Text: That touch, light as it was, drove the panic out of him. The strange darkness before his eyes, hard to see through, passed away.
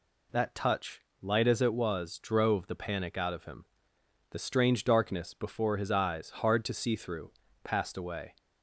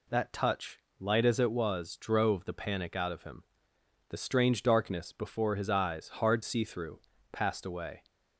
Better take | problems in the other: first | skips "to"; at 6.4 s

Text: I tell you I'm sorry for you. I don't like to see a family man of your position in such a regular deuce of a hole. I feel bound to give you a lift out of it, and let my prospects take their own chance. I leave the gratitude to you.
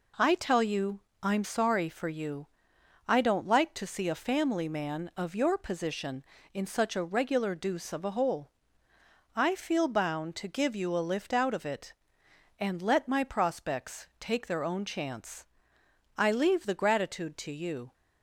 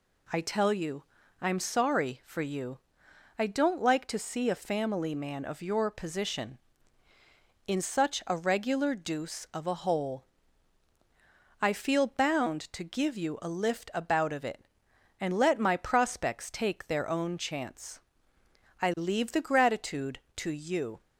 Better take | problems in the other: first | pauses between "you" and "I'm"; slight; at 1.0 s; 0.36 s long; slight in the first // says "about" for "out"; at 13.9 s

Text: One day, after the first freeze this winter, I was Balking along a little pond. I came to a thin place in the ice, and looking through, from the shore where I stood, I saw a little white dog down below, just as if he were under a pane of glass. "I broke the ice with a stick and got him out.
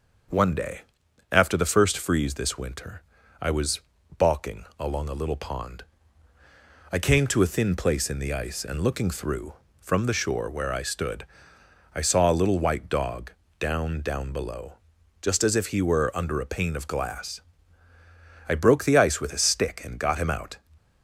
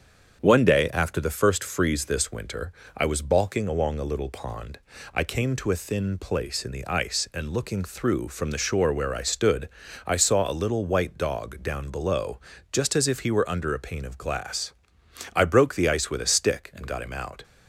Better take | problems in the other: second | starts louder than the rest; until 1.8 s; 6.5 dB; strong in the second // pauses between "was" and "Balking"; at 3.7 s; 0.38 s long // pauses between "dog" and "down"; slight; at 13.3 s; 0.28 s long // says "down" twice; at 14.0 s

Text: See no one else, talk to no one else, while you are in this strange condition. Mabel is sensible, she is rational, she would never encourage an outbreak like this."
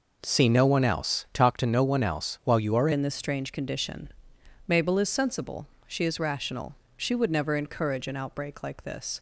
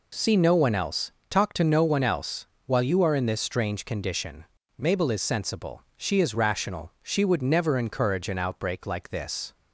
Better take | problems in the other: second | changes voice at "in"; from 2.9 s on; 6.2 s long

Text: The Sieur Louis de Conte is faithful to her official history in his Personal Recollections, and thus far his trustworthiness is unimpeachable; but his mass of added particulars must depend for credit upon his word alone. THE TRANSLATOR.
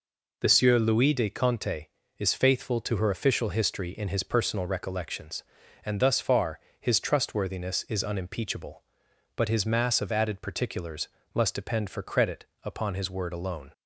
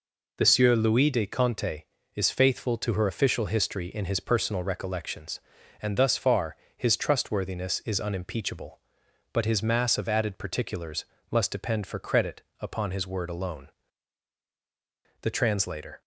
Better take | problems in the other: second | pauses between "far" and "his"; slight; at 6.5 s; 0.20 s long; slight in the second // pauses between "particulars" and "must"; slight; at 11.0 s; 0.24 s long; slight in the second // pauses between "credit" and "upon"; slight; at 12.4 s; 0.18 s long; slight in the second // stops before "THE TRANSLATOR"; at 13.7 s

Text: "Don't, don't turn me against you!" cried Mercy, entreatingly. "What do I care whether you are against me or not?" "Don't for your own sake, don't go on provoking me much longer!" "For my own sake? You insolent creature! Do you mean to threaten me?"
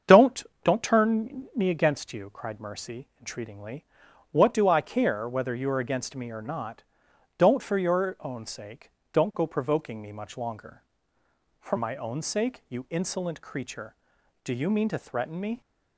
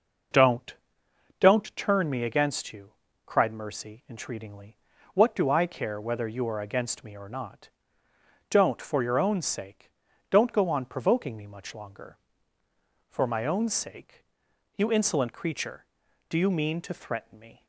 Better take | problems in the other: second | starts louder than the rest; strong; until 1.2 s; 7.5 dB // skips "on"; at 9.4 s

